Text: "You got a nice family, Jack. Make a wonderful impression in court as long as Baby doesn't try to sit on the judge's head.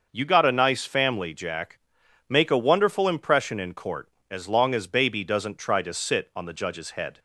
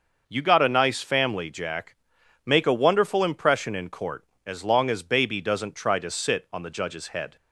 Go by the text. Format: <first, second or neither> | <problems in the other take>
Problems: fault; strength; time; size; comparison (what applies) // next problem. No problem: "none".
neither | starts louder than the rest; noticeable; the same in both